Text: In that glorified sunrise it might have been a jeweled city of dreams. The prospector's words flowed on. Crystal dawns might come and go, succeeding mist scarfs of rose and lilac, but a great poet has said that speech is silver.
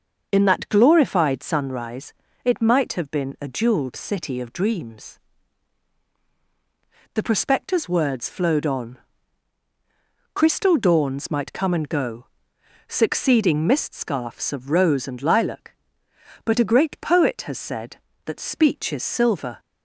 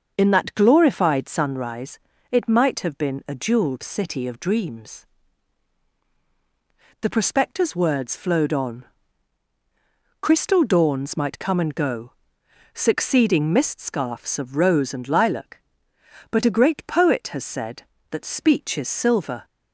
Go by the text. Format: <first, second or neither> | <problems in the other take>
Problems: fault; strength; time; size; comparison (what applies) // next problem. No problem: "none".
neither | starts louder than the rest; the same in both // pauses between "sunrise" and "it"; slight; the same in both